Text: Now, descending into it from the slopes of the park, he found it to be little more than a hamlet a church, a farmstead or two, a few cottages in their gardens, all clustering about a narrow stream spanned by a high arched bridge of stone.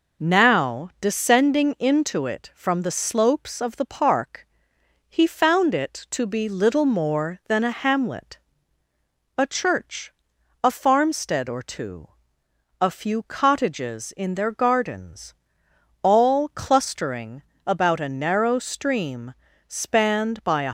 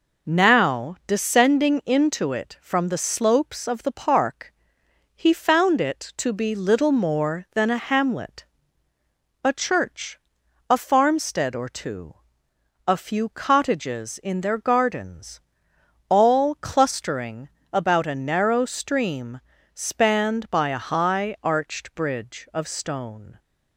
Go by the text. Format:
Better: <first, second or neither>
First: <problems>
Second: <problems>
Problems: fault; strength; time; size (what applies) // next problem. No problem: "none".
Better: second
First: pauses between "hamlet" and "a"; noticeable; at 8.3 s; 0.98 s long // pauses between "clustering" and "about"; slight; at 17.4 s; 0.24 s long // pauses between "stream" and "spanned"; slight; at 19.3 s; 0.32 s long // stops before "high arched bridge of stone"; at 20.6 s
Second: pauses between "hamlet" and "a"; noticeable; at 8.4 s; 0.98 s long // pauses between "clustering" and "about"; slight; at 17.4 s; 0.24 s long // pauses between "stream" and "spanned"; slight; at 19.4 s; 0.32 s long